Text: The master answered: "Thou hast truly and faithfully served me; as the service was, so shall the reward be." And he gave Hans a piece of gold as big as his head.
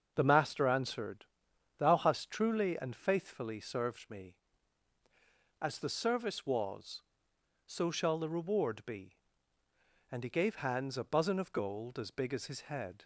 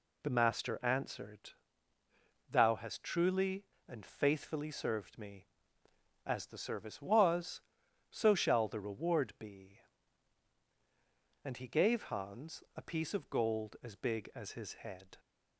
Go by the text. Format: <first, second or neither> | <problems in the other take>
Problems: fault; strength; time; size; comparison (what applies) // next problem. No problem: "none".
second | starts louder than the rest; until 1.1 s; 6.5 dB // says "buzzin" for "piece"; at 11.0 s